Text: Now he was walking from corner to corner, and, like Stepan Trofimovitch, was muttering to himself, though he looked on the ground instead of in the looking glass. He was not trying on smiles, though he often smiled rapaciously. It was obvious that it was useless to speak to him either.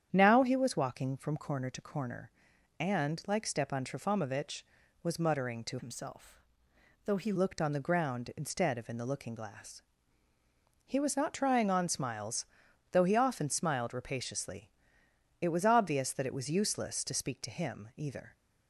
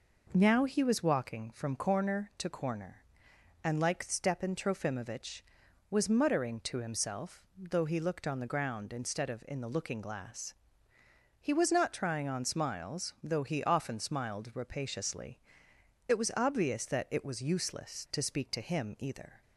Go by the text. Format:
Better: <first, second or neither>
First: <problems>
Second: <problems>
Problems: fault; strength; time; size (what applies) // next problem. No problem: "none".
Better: second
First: starts louder than the rest; strong; until 1.1 s; 9 dB // changes voice from "himself" to "he"; from 5.7 to 7.3 s; 1.6 s long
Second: none